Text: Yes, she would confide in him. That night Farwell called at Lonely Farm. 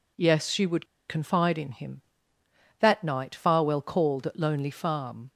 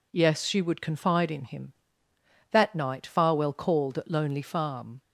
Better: second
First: pauses between "would" and "confide"; slight; at 0.8 s; 0.22 s long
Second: none

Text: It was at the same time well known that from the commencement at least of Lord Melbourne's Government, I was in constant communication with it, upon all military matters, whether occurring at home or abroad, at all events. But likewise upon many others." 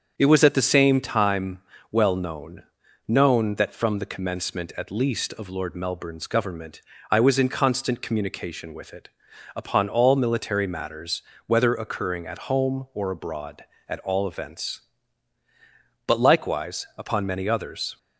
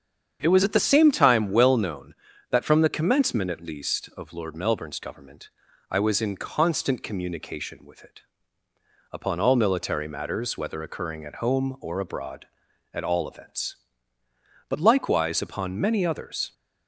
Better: second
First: starts louder than the rest; strong; until 1.1 s; 7 dB // pauses between "time" and "well"; slight; at 1.5 s; 0.30 s long // says "known" twice; at 3.0 s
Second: starts louder than the rest; strong; until 1.4 s; 8 dB

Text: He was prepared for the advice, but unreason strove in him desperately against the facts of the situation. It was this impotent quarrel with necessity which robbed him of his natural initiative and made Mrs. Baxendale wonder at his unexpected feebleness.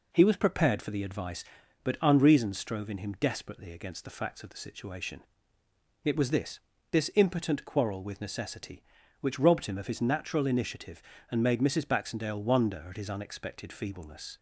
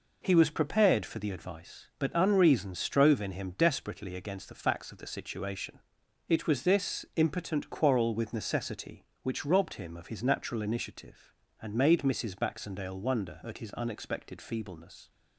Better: second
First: says "this" twice; at 6.9 s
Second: none

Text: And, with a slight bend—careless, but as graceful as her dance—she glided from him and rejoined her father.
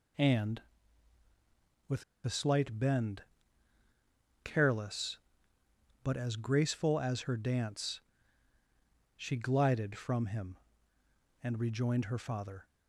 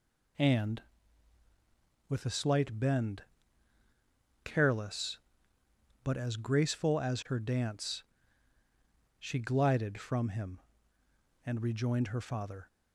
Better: second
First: pauses between "with" and "a"; slight; at 2.0 s; 0.20 s long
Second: none

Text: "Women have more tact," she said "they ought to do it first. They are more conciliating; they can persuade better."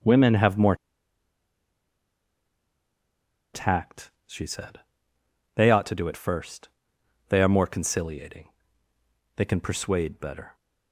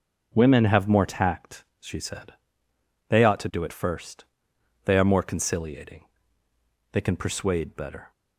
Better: second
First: starts louder than the rest; until 3.8 s; 6.5 dB // pauses between "more" and "tact"; strong; at 0.7 s; 2.7 s long // pauses between "said" and "they"; noticeable; at 4.7 s; 0.76 s long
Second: starts louder than the rest; until 1.3 s; 6 dB // pauses between "said" and "they"; noticeable; at 2.3 s; 0.76 s long

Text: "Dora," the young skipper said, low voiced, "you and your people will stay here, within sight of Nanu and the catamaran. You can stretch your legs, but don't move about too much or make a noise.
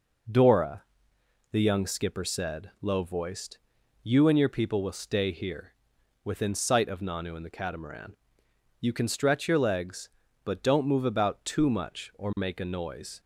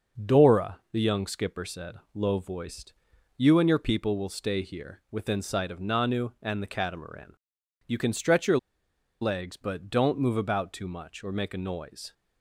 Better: first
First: none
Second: starts louder than the rest; noticeable; until 1.3 s; 6 dB // pauses between "your" and "legs"; noticeable; at 8.5 s; 0.64 s long

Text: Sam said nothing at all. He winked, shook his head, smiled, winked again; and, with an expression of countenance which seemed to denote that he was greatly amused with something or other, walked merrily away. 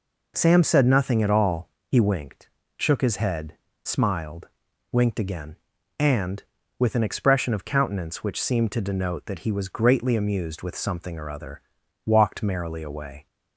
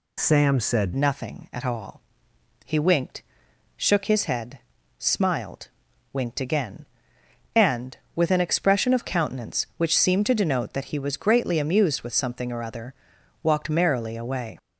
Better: first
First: none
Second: changes voice at "nothing"; from 0.9 s on; 13.6 s long

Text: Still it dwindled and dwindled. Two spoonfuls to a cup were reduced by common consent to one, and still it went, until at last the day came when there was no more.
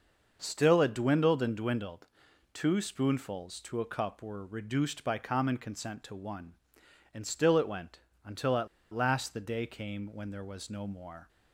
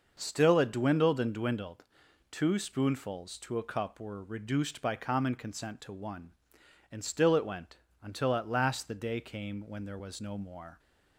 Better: second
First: starts louder than the rest; noticeable; until 1.4 s; 6 dB // pauses between "at" and "last"; slight; at 8.6 s; 0.26 s long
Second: none

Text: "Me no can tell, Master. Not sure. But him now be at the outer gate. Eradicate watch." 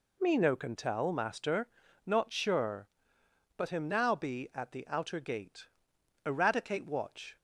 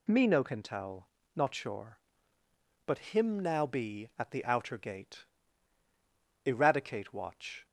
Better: first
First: none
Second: skips "Master"; at 1.2 s

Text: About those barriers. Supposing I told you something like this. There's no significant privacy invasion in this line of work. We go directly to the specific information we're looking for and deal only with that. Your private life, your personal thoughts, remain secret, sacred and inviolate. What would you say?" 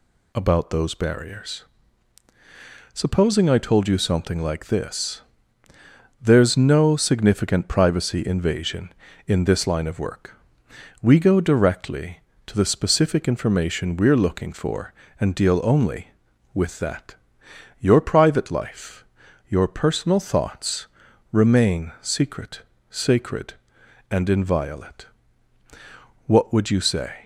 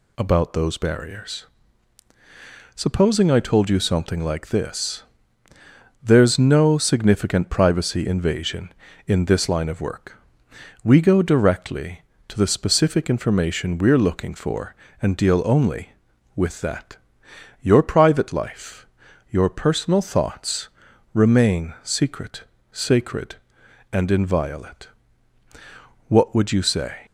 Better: neither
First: none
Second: none

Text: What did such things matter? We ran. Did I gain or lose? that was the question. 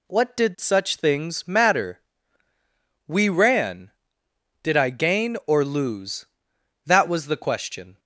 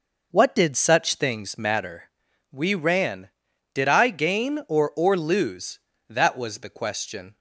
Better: first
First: none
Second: says "or" twice; at 4.9 s

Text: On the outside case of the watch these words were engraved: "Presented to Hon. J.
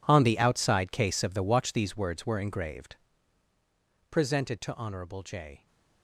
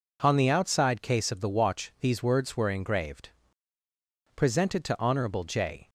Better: second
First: gets quieter; strong; throughout; 16.5 dB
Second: none

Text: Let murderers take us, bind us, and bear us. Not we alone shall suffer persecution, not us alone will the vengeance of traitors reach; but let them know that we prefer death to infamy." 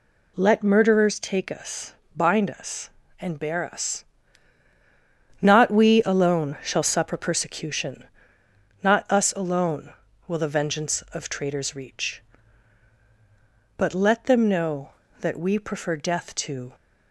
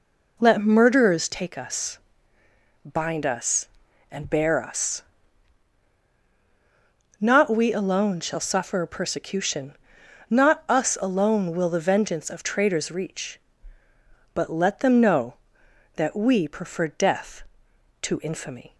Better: second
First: stops before "infamy"; at 16.7 s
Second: none

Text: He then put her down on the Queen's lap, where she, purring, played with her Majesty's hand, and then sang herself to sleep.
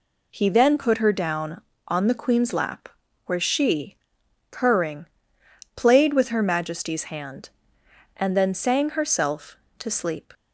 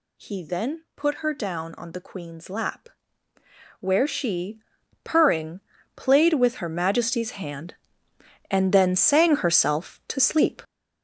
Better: first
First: none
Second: gets louder; strong; throughout; 9 dB

